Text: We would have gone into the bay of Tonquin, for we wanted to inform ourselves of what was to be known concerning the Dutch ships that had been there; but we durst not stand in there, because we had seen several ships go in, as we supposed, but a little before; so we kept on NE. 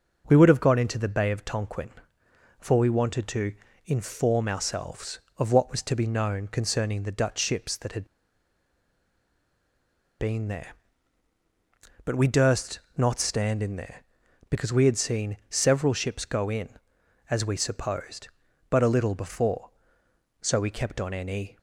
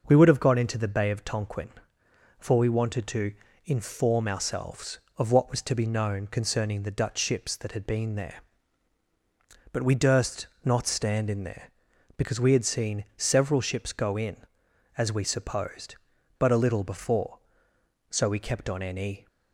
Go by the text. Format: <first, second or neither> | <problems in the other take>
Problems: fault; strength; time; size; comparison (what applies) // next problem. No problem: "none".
second | starts louder than the rest; noticeable; until 1.2 s; 6 dB; noticeable in the second // pauses between "to" and "inform"; slight; at 3.5 s; 0.32 s long; slight in the second // pauses between "had" and "been"; strong; at 8.0 s; 2.1 s long // pauses between "durst" and "not"; slight; at 12.7 s; 0.18 s long; slight in the second